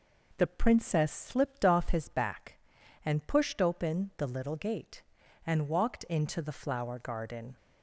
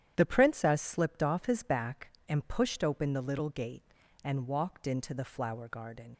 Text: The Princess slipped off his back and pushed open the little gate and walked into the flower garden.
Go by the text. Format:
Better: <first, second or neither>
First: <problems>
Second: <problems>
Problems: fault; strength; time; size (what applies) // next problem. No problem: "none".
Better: first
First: none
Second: starts louder than the rest; strong; until 1.1 s; 10 dB // leaves "garden" unfinished; at 6.1 s; 65 ms